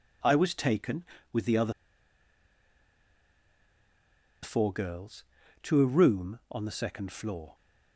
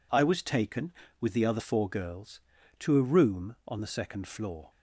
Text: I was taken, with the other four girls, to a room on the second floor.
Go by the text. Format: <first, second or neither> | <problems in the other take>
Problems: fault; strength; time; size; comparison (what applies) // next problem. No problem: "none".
second | pauses between "other" and "four"; strong; at 1.7 s; 2.7 s long